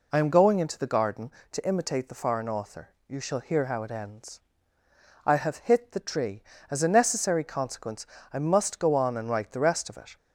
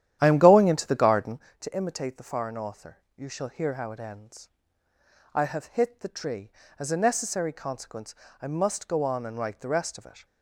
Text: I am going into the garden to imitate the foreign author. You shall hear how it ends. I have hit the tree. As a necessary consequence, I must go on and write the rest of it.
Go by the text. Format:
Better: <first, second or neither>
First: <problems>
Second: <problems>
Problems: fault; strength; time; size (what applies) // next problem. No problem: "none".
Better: first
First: none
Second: starts louder than the rest; strong; until 1.5 s; 11 dB